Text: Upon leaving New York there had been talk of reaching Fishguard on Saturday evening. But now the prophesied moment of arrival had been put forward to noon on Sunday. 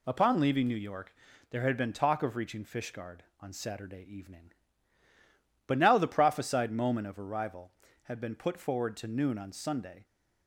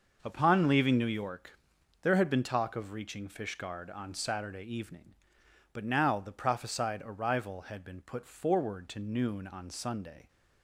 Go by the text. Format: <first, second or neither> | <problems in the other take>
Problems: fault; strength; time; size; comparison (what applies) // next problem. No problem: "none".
first | starts louder than the rest; noticeable; until 1.2 s; 6 dB // pauses between "York" and "there"; noticeable; at 1.5 s; 0.50 s long; slight in the first // skips "moment of"; at 7.0 s